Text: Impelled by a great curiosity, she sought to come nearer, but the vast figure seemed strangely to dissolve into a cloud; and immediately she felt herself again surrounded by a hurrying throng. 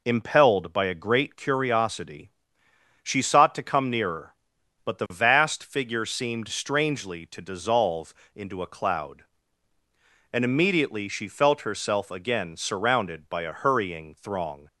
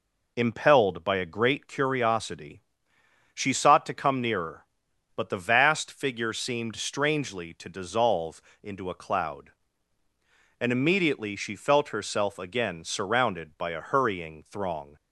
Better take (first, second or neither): neither